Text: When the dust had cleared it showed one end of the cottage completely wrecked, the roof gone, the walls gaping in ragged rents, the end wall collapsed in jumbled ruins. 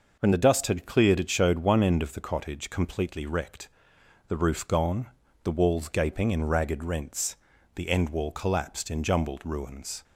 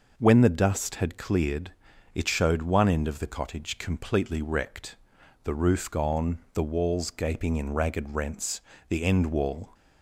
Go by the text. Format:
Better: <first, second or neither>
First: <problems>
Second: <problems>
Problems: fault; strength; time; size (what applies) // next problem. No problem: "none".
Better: first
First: none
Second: pauses between "cleared" and "it"; at 1.7 s; 0.42 s long // stops before "collapsed in jumbled ruins"; at 9.7 s